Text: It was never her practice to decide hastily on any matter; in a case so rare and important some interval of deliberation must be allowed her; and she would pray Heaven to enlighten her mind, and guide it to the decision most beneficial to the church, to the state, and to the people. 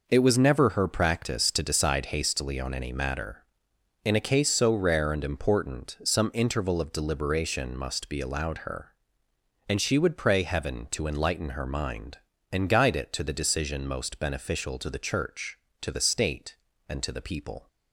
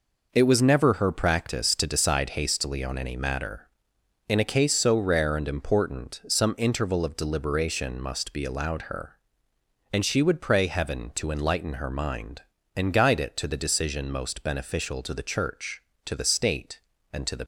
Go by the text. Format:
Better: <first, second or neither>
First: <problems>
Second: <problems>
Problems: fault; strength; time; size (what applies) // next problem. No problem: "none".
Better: first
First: none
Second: stops before "people"; at 17.4 s